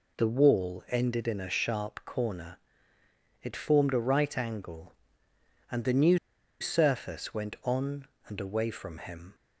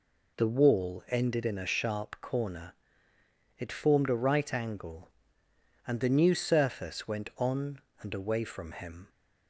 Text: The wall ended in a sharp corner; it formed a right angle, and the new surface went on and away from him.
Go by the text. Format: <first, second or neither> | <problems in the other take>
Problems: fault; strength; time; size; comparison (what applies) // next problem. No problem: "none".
second | pauses between "new" and "surface"; at 6.1 s; 0.42 s long